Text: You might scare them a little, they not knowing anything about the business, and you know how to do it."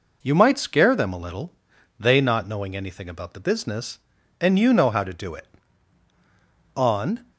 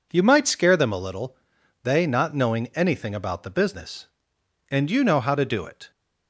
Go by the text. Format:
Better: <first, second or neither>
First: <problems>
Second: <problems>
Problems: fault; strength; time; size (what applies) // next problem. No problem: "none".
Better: second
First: goes on to say "On"; from 6.7 s on; 0.54 s long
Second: none